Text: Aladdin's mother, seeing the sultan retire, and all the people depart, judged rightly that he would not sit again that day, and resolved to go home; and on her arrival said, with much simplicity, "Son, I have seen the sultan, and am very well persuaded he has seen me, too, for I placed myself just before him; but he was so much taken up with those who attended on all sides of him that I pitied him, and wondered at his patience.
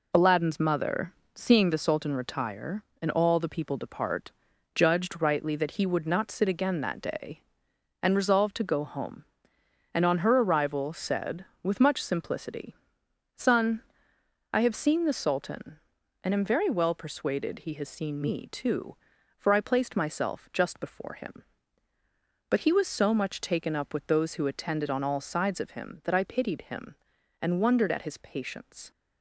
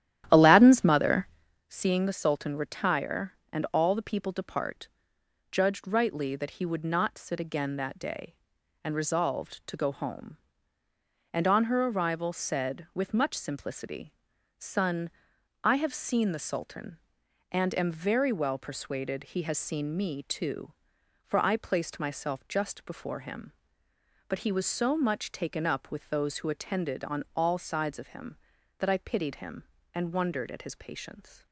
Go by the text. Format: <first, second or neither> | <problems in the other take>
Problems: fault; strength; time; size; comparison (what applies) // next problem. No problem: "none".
first | starts louder than the rest; strong; until 1.7 s; 12 dB